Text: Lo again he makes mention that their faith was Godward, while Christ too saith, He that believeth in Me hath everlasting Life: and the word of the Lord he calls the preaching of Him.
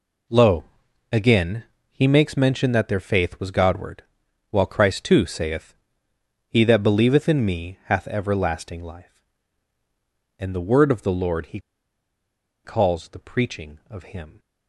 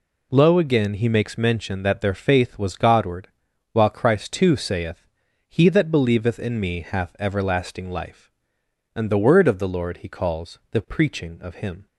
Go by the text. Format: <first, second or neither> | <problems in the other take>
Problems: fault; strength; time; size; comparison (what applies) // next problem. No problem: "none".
second | pauses between "Lo" and "again"; noticeable; at 0.6 s; 0.48 s long // pauses between "again" and "he"; slight; at 1.6 s; 0.26 s long // pauses between "he" and "calls"; at 11.5 s; 1.0 s long